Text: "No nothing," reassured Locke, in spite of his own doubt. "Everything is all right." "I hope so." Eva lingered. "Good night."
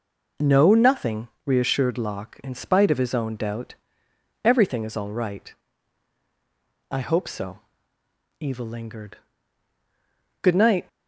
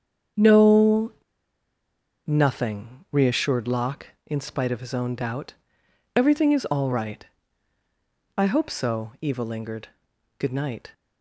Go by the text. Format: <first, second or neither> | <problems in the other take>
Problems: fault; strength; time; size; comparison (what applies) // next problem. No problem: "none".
first | starts louder than the rest; strong; until 2.5 s; 7.5 dB // pauses between "No" and "nothing"; at 1.1 s; 1.1 s long